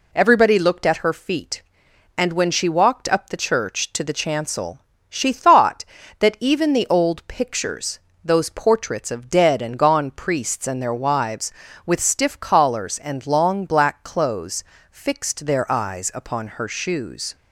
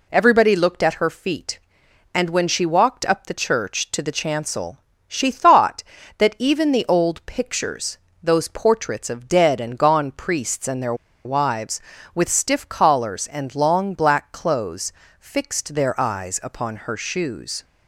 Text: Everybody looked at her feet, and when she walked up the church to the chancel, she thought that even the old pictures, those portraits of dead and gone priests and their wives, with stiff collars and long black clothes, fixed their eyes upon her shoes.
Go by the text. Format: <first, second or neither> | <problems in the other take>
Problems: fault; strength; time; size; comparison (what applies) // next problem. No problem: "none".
first | pauses between "their" and "wives"; slight; at 10.9 s; 0.30 s long